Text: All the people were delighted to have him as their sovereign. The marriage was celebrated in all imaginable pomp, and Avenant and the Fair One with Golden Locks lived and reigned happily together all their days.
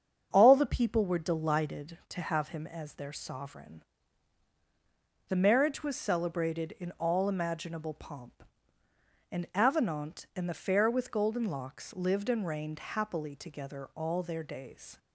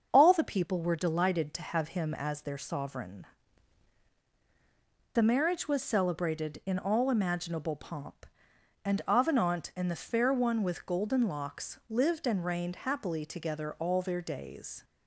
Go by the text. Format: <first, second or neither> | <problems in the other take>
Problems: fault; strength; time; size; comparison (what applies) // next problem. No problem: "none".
second | starts louder than the rest; strong; until 1.3 s; 7 dB; also in the second // skips "One"; at 10.8 s